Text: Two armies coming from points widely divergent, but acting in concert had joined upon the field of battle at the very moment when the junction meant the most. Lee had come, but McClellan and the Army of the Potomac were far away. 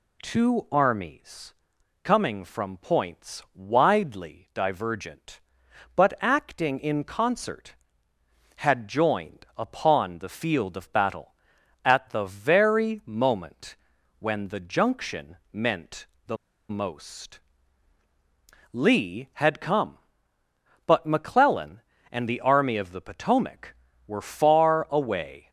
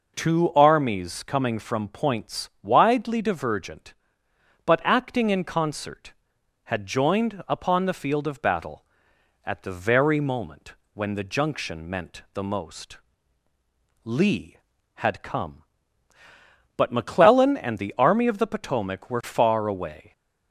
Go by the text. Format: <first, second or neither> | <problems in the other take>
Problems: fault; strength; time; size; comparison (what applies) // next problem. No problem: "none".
second | pauses between "armies" and "coming"; noticeable; at 1.5 s; 0.48 s long // pauses between "moment" and "when"; at 13.7 s; 0.44 s long; slight in the second // pauses between "junction" and "meant"; slight; at 15.3 s; 0.16 s long // pauses between "meant" and "the"; slight; at 16.0 s; 0.22 s long // pauses between "the" and "most"; slight; at 16.3 s; 0.34 s long